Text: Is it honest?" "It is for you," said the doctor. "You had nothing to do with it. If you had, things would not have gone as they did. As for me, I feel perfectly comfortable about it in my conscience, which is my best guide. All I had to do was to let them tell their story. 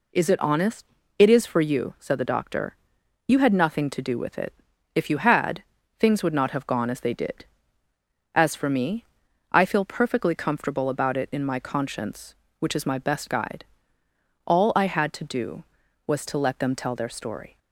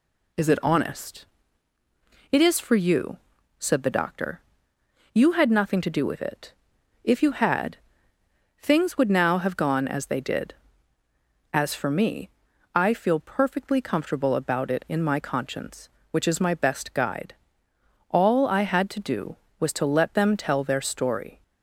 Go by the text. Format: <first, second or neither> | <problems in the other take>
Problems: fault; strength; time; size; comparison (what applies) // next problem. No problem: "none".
first | says "now" for "not"; at 9.1 s